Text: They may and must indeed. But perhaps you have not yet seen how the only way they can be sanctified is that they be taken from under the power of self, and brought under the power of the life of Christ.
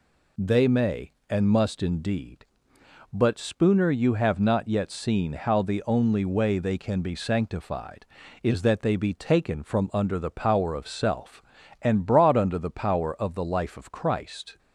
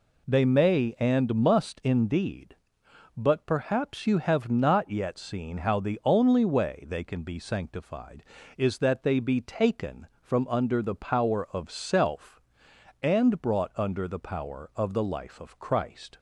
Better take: second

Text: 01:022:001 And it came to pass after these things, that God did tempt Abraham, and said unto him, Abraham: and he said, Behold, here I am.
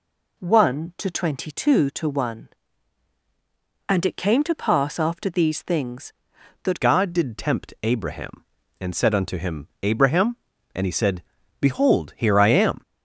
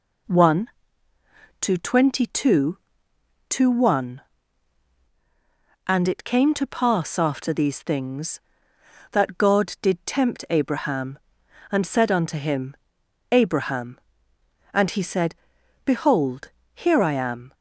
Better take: second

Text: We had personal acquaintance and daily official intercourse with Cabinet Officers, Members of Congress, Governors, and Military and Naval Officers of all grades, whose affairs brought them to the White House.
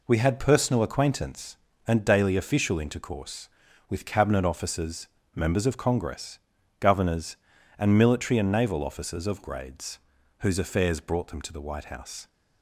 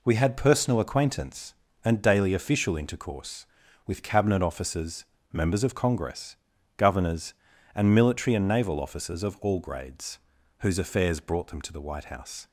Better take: second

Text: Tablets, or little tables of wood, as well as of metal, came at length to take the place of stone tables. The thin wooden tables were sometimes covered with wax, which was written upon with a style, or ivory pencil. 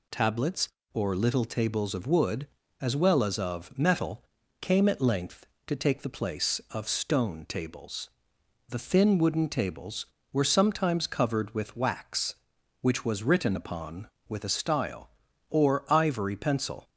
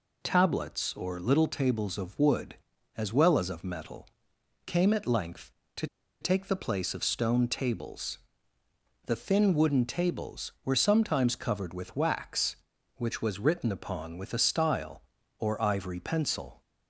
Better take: first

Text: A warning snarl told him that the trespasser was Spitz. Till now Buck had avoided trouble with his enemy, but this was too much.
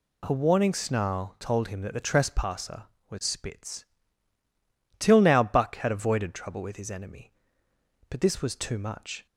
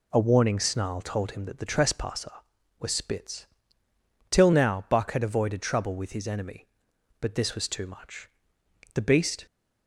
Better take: first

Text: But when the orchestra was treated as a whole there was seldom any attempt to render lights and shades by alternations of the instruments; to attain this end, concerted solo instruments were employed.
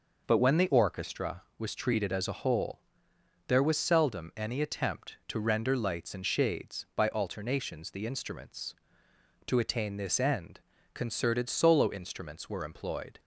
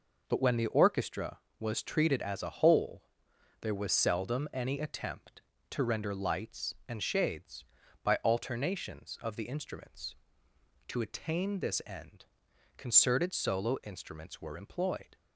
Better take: second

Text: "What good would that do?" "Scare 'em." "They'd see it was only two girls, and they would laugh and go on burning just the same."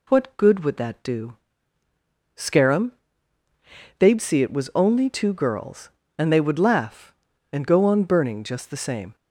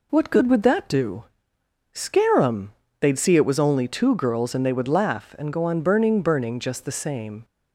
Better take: first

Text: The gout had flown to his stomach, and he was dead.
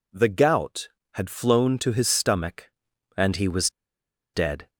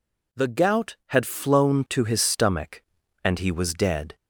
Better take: second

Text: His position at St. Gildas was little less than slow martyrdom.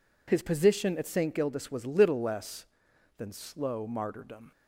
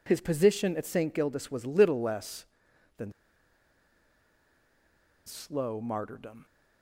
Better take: first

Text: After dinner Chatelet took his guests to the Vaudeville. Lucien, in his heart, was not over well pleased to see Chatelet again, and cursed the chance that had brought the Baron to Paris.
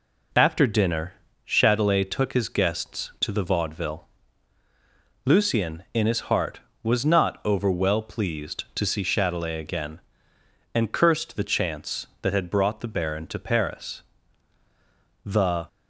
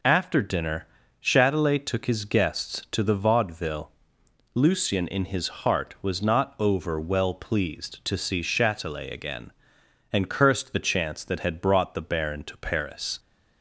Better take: second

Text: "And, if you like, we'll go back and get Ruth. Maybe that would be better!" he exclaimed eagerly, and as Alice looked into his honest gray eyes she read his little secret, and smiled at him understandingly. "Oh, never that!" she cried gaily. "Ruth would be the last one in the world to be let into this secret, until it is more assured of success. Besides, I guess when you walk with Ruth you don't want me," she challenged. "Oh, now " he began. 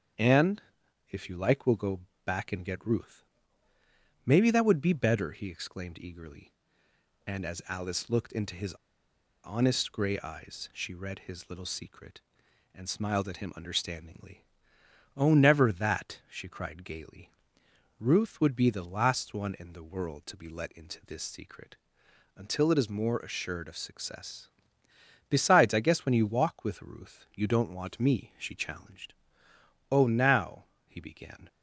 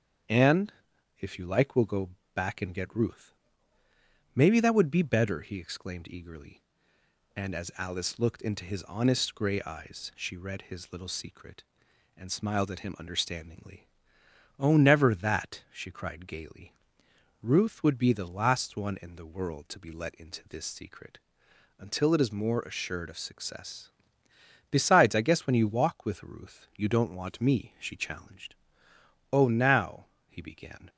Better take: second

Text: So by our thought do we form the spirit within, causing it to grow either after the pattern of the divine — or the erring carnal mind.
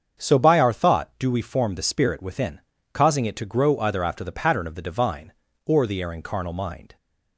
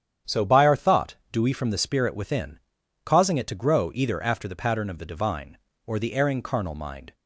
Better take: first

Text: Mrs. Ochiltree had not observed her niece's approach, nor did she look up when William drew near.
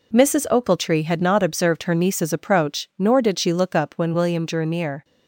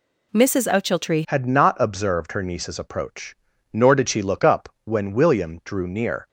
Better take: first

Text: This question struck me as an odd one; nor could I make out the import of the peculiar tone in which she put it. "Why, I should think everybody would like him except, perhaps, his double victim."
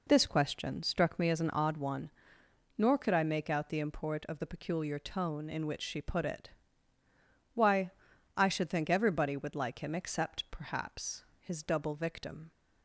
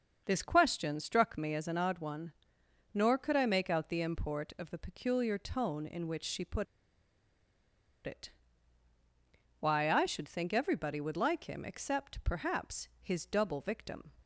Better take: first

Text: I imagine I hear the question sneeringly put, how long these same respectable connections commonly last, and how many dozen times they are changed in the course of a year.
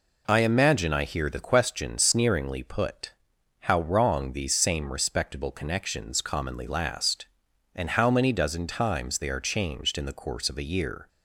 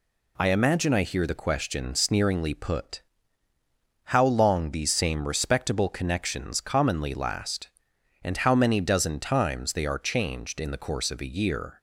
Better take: second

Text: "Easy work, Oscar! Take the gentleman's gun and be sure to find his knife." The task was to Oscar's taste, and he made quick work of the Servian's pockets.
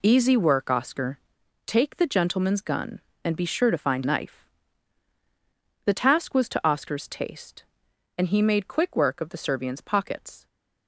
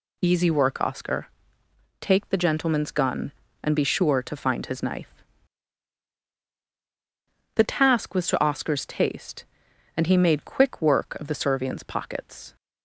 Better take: second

